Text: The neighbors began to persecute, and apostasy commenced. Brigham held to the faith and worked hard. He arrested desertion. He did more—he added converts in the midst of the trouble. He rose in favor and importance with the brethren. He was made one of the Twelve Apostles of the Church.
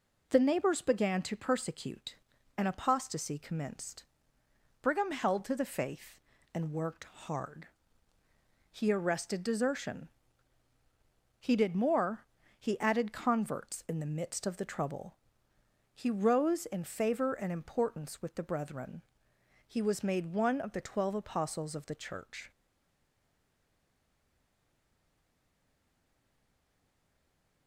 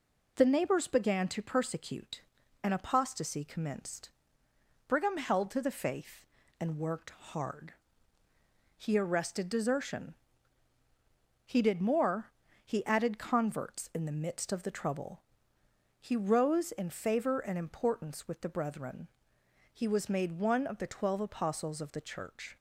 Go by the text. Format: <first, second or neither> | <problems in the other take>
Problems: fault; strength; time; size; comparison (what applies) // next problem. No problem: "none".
second | stays silent after the last word; strong; from 22.5 s on; 5.1 s long